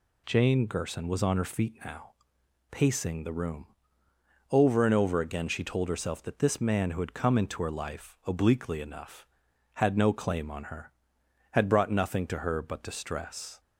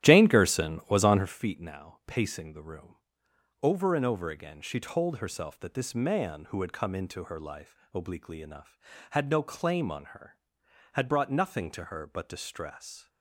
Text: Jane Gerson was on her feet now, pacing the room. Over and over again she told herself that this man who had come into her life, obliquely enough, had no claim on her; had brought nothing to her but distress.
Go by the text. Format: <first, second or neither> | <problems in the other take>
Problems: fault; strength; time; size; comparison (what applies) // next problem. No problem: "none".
first | starts louder than the rest; strong; until 1.3 s; 12.5 dB